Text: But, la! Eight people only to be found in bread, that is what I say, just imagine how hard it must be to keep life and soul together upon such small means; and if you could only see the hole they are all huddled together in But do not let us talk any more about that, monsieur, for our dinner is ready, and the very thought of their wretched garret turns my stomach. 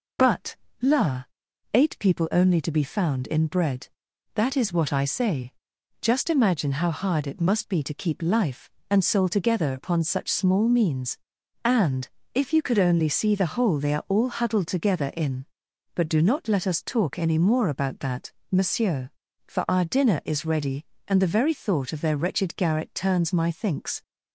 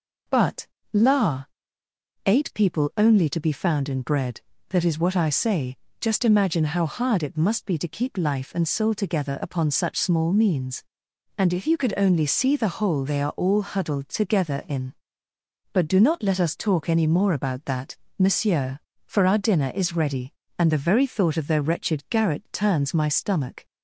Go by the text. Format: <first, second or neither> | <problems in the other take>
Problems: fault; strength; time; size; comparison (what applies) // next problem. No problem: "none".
second | pauses between "and" and "if"; slight; at 12.0 s; 0.28 s long // says "thinks" for "stomach"; at 23.5 s